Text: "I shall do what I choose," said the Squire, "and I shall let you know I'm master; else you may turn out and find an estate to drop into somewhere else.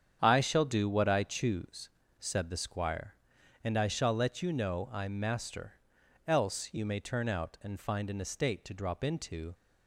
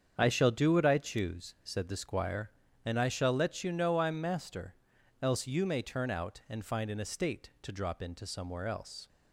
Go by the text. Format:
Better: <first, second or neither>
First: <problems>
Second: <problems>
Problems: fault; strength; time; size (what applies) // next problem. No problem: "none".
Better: second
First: starts louder than the rest; strong; until 1.2 s; 8 dB // stops before "somewhere else"; at 9.5 s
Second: starts louder than the rest; strong; until 1.1 s; 7.5 dB